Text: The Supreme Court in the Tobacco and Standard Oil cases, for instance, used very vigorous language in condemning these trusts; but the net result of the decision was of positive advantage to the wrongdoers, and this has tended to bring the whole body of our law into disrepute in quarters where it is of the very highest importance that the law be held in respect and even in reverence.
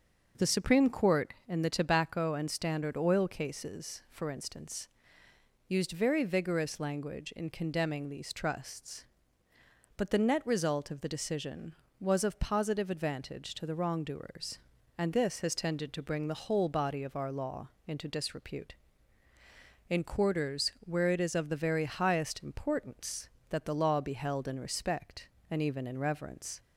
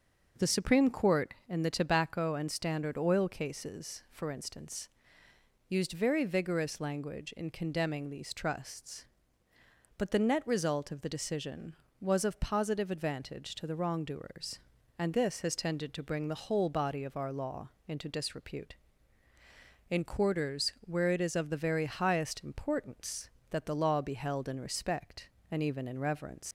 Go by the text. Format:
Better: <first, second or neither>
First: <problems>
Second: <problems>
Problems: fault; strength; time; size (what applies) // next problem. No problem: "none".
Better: first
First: starts louder than the rest; noticeable; until 1.5 s; 6 dB // pauses between "law" and "into"; slight; at 17.6 s; 0.16 s long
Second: starts louder than the rest; noticeable; until 1.5 s; 6 dB // pauses between "law" and "into"; slight; at 17.7 s; 0.16 s long // leaves "reverence" unfinished; at 26.4 s; 95 ms